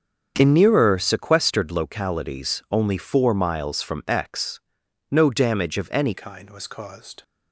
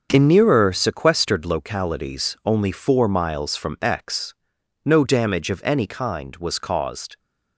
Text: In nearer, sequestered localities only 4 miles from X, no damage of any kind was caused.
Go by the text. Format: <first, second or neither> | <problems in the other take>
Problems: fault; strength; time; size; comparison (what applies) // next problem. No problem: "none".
second | starts louder than the rest; strong; until 1.3 s; 7.5 dB; also in the second // changes voice at "kind"; from 6.1 s on; 1.1 s long